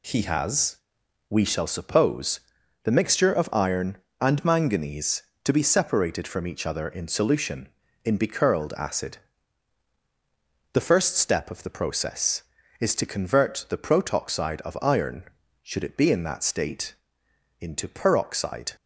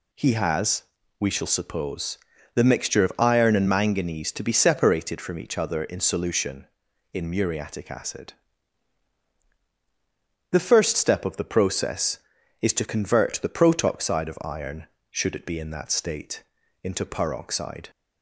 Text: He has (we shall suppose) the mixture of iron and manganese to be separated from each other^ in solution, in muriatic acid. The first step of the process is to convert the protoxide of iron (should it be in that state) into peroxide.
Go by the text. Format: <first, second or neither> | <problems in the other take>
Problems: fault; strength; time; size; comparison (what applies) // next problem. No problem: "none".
second | says "becurled" for "muriatic"; at 8.1 s